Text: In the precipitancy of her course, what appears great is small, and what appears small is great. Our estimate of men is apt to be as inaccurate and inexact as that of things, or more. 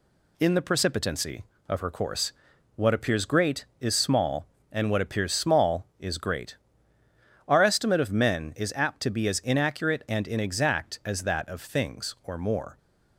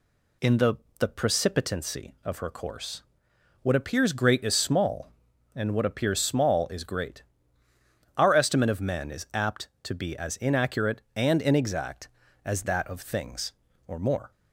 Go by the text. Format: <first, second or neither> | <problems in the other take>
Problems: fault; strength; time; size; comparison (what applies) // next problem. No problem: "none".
first | says "the" twice; at 0.9 s